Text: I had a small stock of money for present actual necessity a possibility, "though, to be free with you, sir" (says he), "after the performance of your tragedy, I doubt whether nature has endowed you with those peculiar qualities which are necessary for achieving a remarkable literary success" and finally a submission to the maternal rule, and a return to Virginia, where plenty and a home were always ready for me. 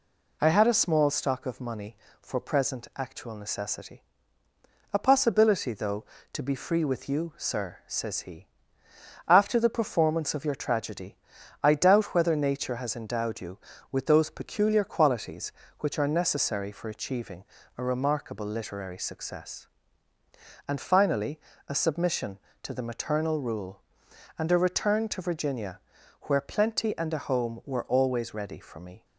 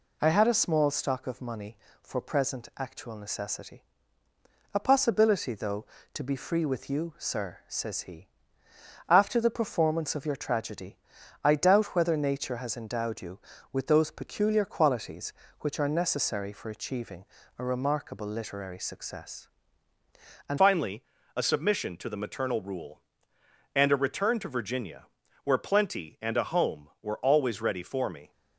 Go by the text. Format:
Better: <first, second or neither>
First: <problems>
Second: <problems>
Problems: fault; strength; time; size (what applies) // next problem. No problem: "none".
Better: first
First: pauses between "necessity" and "a"; noticeable; at 4.0 s; 0.90 s long // pauses between "achieving" and "a"; slight; at 17.4 s; 0.32 s long // pauses between "finally" and "a"; slight; at 21.3 s; 0.30 s long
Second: pauses between "necessity" and "a"; noticeable; at 3.8 s; 0.90 s long // pauses between "achieving" and "a"; slight; at 17.2 s; 0.32 s long // changes voice at "finally"; from 20.5 s on; 7.8 s long // pauses between "finally" and "a"; slight; at 21.0 s; 0.32 s long